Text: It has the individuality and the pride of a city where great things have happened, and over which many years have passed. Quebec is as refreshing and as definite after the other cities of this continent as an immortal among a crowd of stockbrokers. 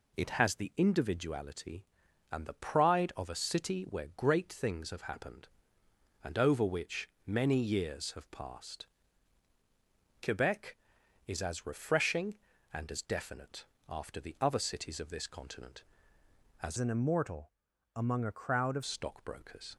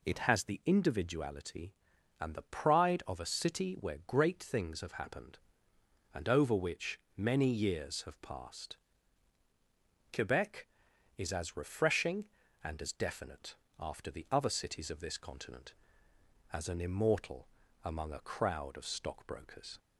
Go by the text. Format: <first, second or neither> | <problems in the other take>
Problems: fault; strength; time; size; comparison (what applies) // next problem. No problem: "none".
second | pauses between "which" and "many"; slight; at 7.0 s; 0.18 s long; slight in the second // pauses between "definite" and "after"; slight; at 13.6 s; 0.24 s long; slight in the second // changes voice from "an" to "of"; from 16.7 to 18.8 s; 2.1 s long // pauses between "immortal" and "among"; at 17.5 s; 0.44 s long; slight in the second